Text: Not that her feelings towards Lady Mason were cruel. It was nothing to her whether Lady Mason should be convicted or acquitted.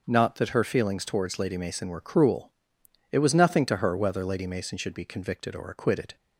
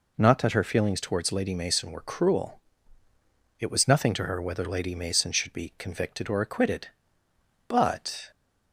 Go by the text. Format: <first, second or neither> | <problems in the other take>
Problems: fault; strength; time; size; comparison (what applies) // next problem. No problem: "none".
first | goes on to say "But"; noticeable; from 7.6 s on; 0.62 s long